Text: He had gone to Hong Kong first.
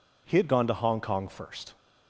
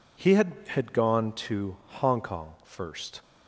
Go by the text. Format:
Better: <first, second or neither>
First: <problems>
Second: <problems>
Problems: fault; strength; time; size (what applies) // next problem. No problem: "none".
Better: first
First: none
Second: says "had" twice; at 0.6 s // pauses between "to" and "Hong"; slight; at 1.7 s; 0.24 s long